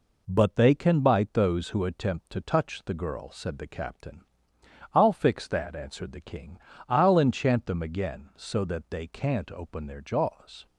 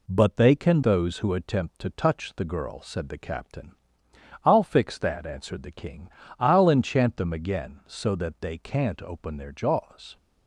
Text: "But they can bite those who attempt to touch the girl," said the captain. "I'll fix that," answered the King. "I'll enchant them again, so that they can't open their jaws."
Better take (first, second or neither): first